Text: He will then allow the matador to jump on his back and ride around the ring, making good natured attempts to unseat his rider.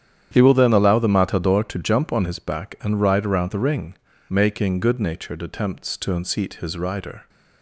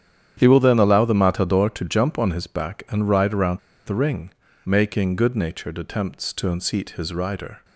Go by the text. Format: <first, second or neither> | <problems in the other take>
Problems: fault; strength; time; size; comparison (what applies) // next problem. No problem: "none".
first | starts louder than the rest; strong; until 1.3 s; 9.5 dB; strong in the first // pauses between "around" and "the"; slight; at 3.5 s; 0.27 s long